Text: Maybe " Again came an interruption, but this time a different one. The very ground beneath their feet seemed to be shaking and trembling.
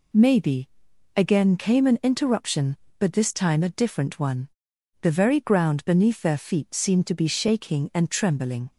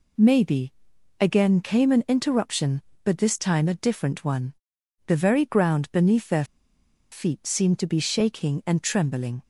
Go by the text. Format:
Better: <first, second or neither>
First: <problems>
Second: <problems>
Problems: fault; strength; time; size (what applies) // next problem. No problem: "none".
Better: first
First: none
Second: pauses between "their" and "feet"; noticeable; at 6.4 s; 0.68 s long